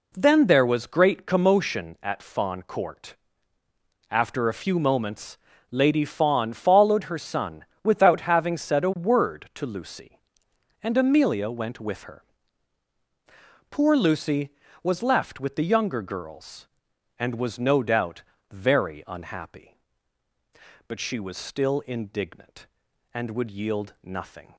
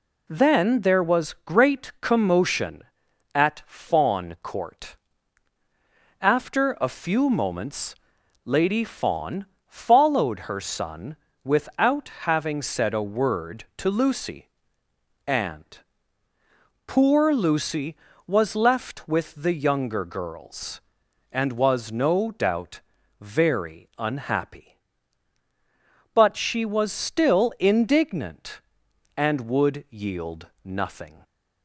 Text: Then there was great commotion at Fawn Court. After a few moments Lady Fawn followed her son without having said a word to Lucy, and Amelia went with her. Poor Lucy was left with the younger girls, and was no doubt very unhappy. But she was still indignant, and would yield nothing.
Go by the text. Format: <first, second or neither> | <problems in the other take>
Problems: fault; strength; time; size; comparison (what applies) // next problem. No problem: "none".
first | pauses between "moments" and "Lady"; noticeable; at 7.9 s; 0.50 s long; slight in the first // pauses between "Fawn" and "followed"; slight; at 9.4 s; 0.20 s long // pauses between "son" and "without"; slight; at 11.1 s; 0.28 s long; slight in the first // pauses between "without" and "having"; slight; at 12.0 s; 0.16 s long // skips "Amelia went with her"; at 16.3 s // pauses between "doubt" and "very"; at 22.8 s; 0.40 s long; slight in the first // pauses between "yield" and "nothing"; slight; at 30.4 s; 0.16 s long